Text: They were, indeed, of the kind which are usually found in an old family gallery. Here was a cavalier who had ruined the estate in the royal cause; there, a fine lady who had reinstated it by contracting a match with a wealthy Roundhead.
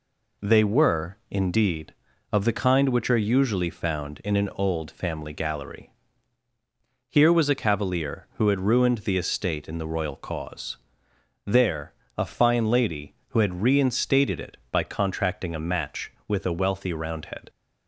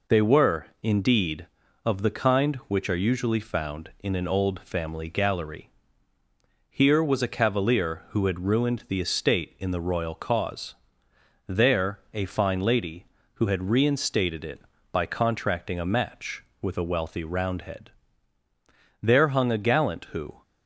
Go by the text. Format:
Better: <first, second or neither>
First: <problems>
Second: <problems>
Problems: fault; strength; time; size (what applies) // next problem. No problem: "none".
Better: first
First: none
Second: goes on to say "There hung a gallant who"; from 18.9 s on; 1.4 s long